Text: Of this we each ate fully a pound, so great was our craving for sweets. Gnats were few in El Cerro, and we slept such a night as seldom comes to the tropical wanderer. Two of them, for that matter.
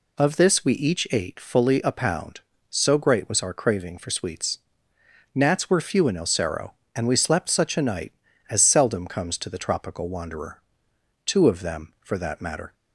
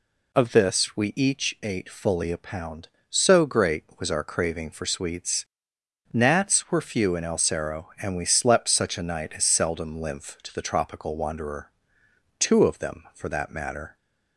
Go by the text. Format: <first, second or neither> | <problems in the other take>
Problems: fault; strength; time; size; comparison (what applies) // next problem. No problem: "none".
first | says "lymph" for "comes"; at 10.0 s